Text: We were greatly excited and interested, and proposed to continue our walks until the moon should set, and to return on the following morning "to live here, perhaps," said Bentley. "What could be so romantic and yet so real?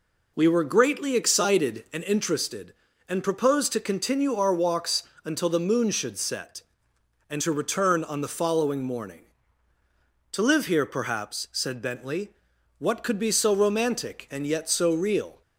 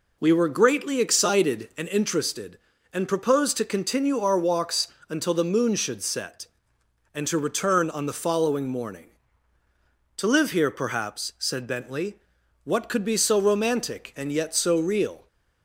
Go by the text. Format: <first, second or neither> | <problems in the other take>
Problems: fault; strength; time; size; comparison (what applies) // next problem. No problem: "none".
neither | pauses between "walks" and "until"; slight; the same in both